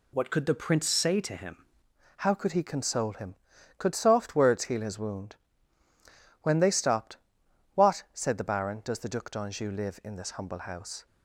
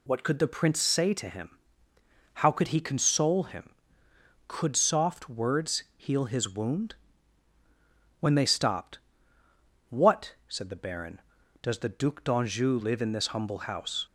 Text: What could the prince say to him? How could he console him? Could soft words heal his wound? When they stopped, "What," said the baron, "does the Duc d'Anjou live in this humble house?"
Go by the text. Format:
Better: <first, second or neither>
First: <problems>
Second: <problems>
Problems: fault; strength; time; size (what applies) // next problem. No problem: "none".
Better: second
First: changes voice at "How"; from 2.1 s on; 8.9 s long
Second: none